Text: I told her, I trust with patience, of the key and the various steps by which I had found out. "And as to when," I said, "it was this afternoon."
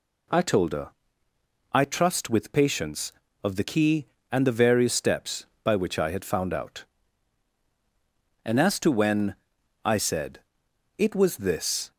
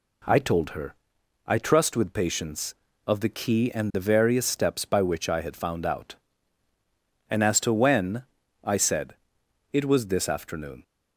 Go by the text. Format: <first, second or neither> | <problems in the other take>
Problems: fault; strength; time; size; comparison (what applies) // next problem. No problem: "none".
second | stops before "afternoon"; at 11.9 s